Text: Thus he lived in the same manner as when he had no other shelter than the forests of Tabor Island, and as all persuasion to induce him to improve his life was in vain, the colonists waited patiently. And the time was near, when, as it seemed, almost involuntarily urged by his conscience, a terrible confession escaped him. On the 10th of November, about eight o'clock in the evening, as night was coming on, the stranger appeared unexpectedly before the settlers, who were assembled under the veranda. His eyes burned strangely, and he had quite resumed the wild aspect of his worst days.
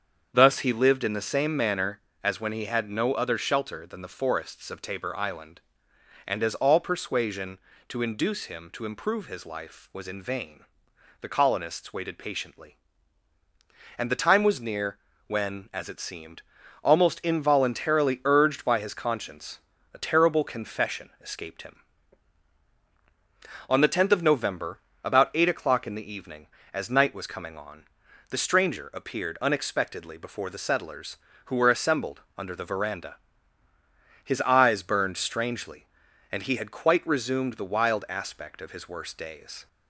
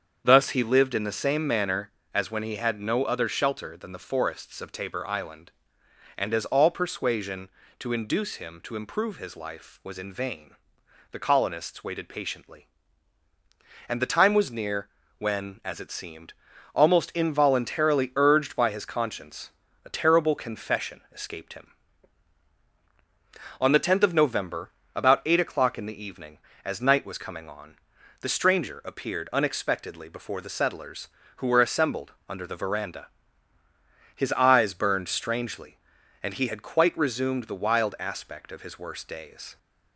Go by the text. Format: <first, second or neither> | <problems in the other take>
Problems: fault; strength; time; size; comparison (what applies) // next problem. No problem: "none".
neither | starts louder than the rest; strong; the same in both // pauses between "assembled" and "under"; slight; the same in both